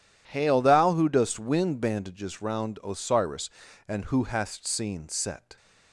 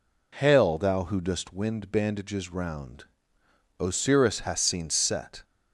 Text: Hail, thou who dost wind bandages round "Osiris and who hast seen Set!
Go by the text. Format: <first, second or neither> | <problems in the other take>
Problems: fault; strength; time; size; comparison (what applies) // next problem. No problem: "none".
first | pauses between "round" and "Osiris"; noticeable; at 3.0 s; 0.76 s long // skips "and who"; at 4.3 s